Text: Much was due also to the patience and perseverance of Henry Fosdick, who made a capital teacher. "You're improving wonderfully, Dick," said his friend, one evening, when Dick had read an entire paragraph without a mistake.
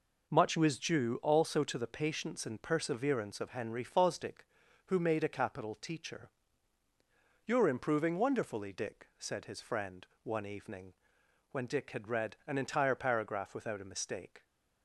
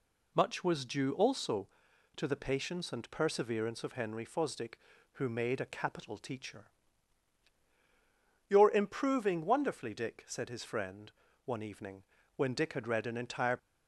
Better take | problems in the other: first | stops before "paragraph without a mistake"; at 13.5 s

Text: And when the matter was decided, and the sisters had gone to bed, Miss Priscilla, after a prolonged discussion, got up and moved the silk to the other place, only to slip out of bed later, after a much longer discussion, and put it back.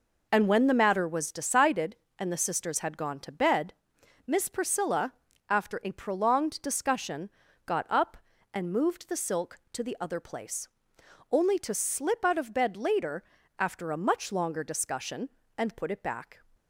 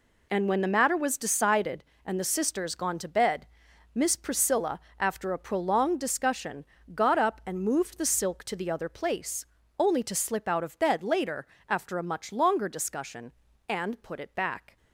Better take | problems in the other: first | skips "had"; at 2.7 s

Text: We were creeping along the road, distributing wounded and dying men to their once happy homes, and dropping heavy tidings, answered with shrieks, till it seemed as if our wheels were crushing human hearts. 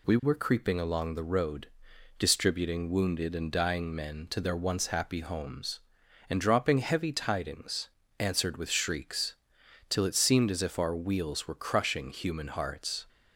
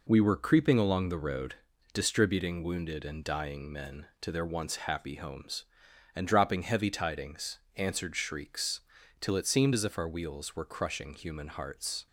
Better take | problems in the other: first | skips "with"; at 8.1 s

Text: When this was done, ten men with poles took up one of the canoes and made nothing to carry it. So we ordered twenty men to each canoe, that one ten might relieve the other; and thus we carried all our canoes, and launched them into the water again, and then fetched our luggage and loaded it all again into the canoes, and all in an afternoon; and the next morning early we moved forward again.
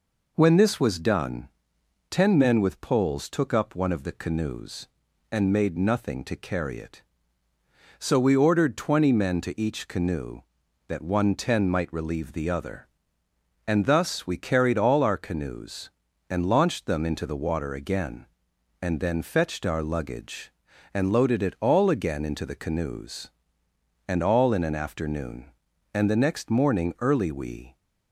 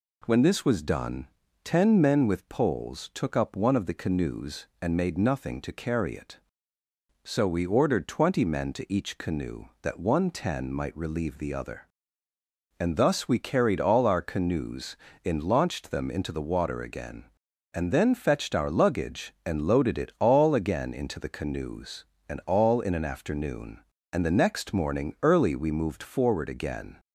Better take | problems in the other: second | stops before "moved forward again"; at 27.7 s

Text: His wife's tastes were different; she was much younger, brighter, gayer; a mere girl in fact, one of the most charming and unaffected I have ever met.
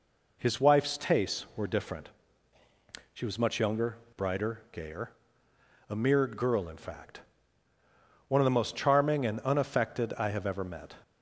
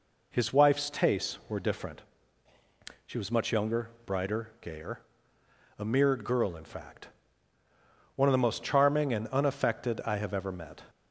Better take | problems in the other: neither | none

